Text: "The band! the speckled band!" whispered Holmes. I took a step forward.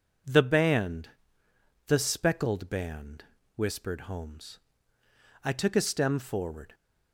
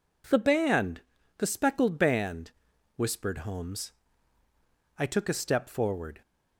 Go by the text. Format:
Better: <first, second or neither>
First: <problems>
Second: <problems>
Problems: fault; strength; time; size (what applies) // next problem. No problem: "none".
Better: second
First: says "stem" for "step"; at 5.8 s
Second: none